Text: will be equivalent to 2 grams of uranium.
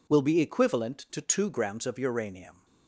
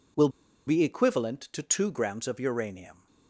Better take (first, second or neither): first